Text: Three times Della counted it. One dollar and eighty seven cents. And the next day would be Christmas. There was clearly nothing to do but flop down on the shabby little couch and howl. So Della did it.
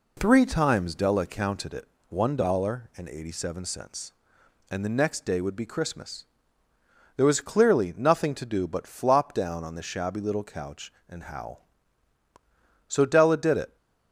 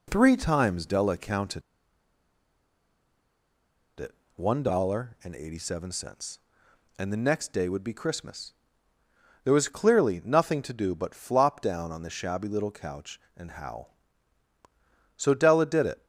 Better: first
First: none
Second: pauses between "counted" and "it"; strong; at 1.6 s; 2.3 s long

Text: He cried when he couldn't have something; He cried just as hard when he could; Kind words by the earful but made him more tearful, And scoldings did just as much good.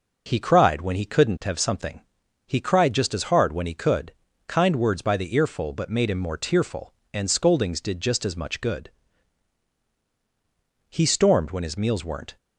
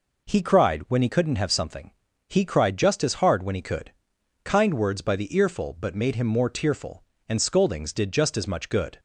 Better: second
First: goes on to say "He stormed when his meals weren't"; from 10.8 s on; 1.4 s long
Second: none

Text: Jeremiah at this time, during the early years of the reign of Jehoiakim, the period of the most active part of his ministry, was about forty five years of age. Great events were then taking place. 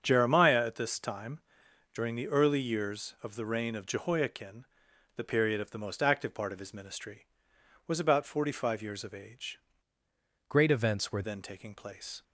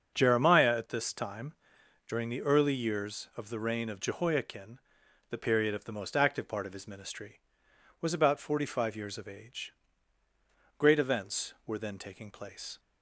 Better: second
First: starts louder than the rest; strong; until 1.0 s; 7 dB // changes voice from "Great" to "were"; from 10.4 to 11.2 s; 0.8 s long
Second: starts louder than the rest; until 1.1 s; 7 dB

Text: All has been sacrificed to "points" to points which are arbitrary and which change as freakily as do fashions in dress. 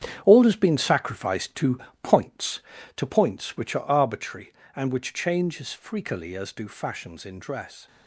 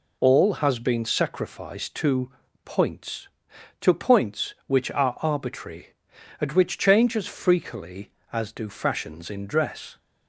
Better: second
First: gets quieter; strong; throughout; 10 dB // pauses between "to" and "points"; slight; at 1.7 s; 0.24 s long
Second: pauses between "to" and "points"; slight; at 2.3 s; 0.32 s long

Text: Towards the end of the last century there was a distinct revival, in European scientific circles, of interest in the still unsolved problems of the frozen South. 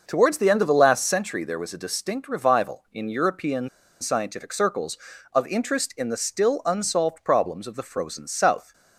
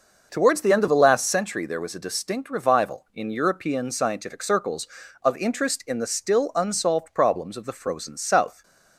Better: second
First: pauses between "European" and "scientific"; slight; at 3.6 s; 0.31 s long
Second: none

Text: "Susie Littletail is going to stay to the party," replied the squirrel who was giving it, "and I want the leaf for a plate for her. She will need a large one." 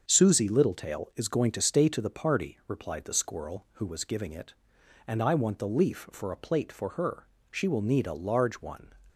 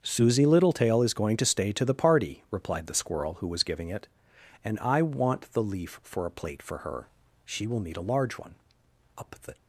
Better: first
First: starts louder than the rest; until 1.0 s; 7 dB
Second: starts louder than the rest; until 1.0 s; 7 dB // goes on to say "Up the"; slight; from 9.1 s on; 0.38 s long

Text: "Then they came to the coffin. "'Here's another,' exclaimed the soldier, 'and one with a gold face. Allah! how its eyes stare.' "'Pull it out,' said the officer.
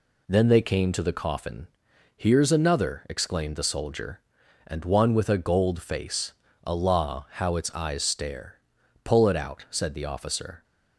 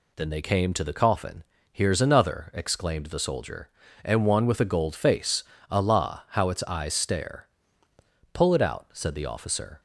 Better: neither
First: none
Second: none

